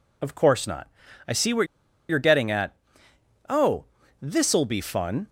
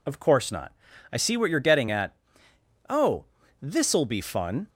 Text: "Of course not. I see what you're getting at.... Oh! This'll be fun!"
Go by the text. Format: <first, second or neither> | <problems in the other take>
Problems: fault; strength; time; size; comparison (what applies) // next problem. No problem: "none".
second | pauses between "what" and "you're"; at 1.6 s; 0.43 s long